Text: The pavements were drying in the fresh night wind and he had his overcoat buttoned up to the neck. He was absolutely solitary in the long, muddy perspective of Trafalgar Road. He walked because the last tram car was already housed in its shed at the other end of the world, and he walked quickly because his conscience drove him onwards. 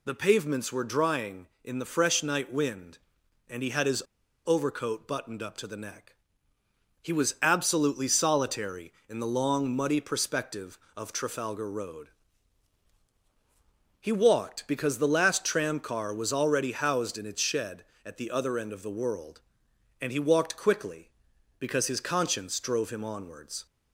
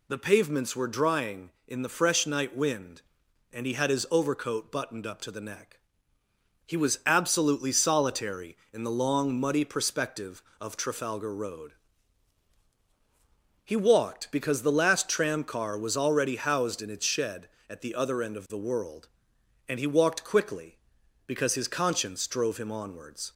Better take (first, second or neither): second